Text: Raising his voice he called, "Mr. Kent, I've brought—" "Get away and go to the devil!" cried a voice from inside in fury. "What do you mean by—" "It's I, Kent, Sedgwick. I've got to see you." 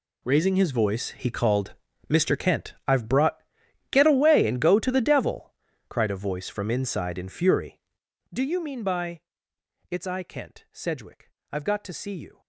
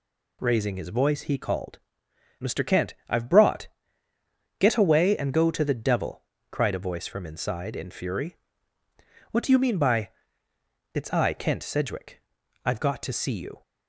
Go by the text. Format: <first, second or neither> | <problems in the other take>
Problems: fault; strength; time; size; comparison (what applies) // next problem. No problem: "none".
second | skips "What"; at 8.0 s